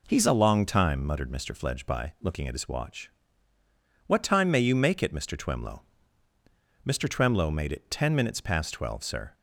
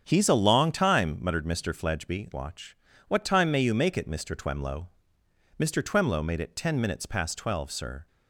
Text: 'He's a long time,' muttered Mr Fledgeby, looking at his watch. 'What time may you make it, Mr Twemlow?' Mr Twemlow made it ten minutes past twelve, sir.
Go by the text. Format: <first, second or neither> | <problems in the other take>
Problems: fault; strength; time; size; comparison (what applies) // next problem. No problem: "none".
first | starts louder than the rest; strong; until 1.0 s; 8 dB // skips "looking at his"; at 2.3 s